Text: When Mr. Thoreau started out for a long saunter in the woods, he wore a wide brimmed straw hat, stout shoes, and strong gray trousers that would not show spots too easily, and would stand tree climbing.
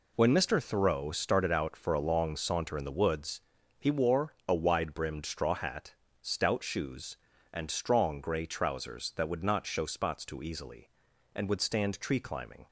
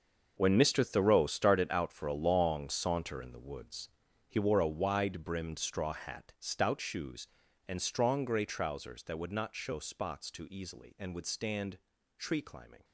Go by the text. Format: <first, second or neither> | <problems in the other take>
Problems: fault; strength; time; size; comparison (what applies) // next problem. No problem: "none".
first | gets quieter; strong; throughout; 13 dB // pauses between "stand" and "tree"; at 11.7 s; 0.38 s long